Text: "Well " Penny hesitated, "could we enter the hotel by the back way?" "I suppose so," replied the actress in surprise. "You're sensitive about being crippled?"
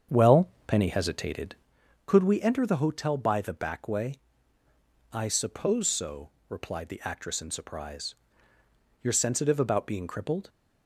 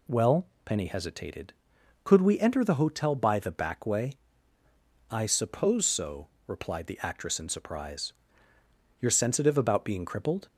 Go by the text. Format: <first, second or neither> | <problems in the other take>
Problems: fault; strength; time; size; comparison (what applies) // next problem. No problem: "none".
second | starts louder than the rest; strong; until 1.7 s; 7.5 dB